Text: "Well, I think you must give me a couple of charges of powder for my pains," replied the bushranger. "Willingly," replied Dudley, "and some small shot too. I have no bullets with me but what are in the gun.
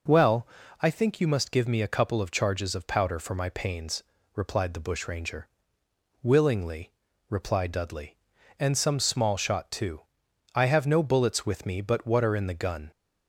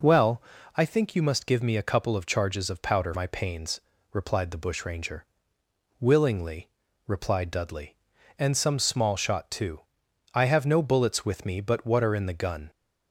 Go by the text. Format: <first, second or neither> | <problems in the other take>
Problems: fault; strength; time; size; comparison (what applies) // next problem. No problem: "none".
first | skips "for"; at 3.1 s